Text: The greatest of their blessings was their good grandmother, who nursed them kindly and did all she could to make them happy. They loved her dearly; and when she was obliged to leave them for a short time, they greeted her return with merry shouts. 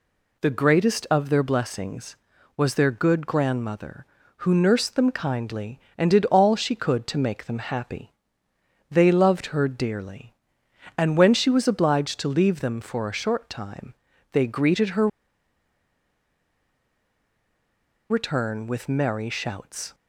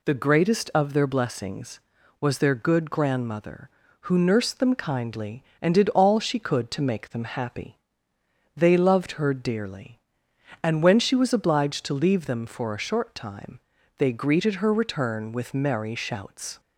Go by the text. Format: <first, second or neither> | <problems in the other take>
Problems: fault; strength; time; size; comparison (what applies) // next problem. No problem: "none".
second | pauses between "her" and "return"; strong; at 15.0 s; 3.0 s long